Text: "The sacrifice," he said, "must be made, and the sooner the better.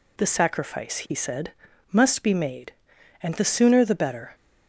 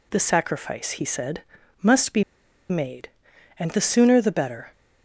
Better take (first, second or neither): first